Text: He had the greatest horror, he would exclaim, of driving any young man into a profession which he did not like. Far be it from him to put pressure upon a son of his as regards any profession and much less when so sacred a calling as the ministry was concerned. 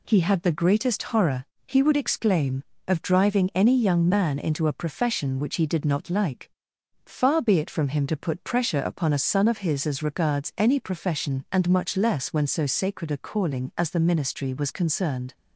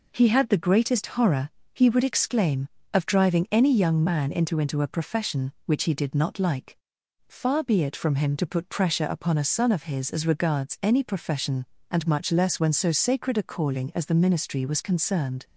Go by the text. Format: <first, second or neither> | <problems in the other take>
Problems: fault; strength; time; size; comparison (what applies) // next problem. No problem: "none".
first | says "into" twice; at 4.5 s